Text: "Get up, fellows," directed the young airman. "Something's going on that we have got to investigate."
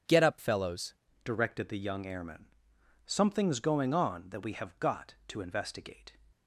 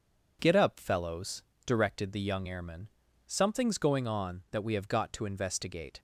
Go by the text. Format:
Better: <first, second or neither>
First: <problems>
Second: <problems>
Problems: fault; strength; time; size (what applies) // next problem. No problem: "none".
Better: second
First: starts louder than the rest; until 1.3 s; 7 dB // changes voice at "directed"; from 1.2 s on; 4.9 s long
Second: none